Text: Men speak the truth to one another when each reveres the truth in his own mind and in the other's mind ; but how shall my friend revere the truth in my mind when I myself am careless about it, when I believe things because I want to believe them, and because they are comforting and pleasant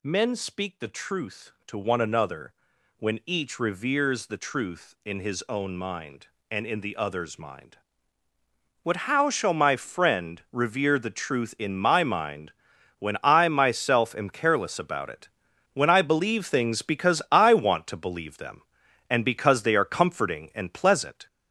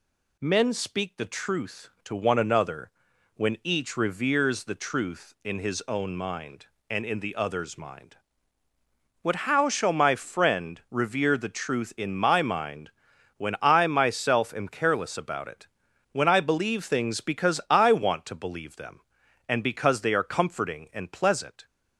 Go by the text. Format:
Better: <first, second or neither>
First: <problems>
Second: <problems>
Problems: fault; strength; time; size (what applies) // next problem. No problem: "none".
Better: second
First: gets louder; noticeable; throughout; 4.5 dB // pauses between "another" and "when"; noticeable; at 2.5 s; 0.46 s long // pauses between "mind" and "when"; noticeable; at 12.5 s; 0.46 s long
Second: pauses between "another" and "when"; noticeable; at 2.8 s; 0.46 s long // pauses between "mind" and "when"; noticeable; at 12.9 s; 0.46 s long